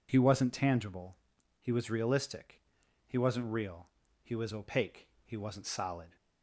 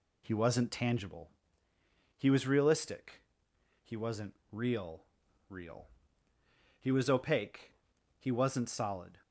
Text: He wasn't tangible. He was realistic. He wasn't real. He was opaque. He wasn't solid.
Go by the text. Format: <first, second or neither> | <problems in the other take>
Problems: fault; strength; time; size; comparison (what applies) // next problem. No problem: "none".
first | pauses between "wasn't" and "real"; slight; at 4.3 s; 0.18 s long // says "real" twice; at 5.5 s